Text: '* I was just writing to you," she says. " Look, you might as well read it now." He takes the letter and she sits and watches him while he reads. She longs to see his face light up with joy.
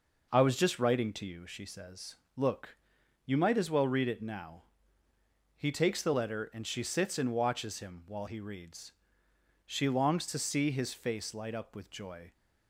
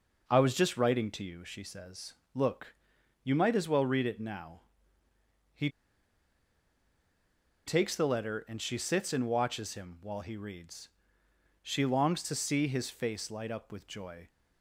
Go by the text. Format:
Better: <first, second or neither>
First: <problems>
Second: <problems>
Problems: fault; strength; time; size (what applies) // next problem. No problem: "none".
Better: first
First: none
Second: pauses between "He" and "takes"; strong; at 5.6 s; 1.9 s long